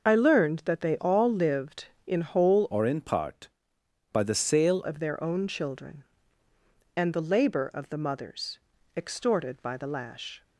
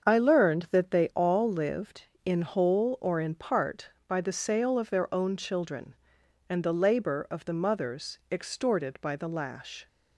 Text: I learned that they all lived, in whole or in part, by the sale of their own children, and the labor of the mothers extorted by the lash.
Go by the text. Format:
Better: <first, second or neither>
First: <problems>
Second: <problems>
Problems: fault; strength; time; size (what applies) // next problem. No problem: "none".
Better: second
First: starts louder than the rest; noticeable; until 1.0 s; 6 dB // changes voice from "or" to "sale"; from 2.7 to 4.8 s; 2.1 s long // pauses between "mothers" and "extorted"; at 8.5 s; 0.38 s long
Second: starts louder than the rest; until 1.1 s; 7 dB